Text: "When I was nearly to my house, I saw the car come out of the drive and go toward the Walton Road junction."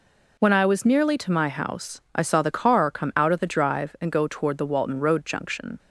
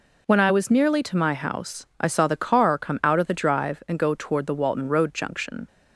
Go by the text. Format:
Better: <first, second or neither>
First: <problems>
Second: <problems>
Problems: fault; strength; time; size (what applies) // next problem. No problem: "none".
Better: neither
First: none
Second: none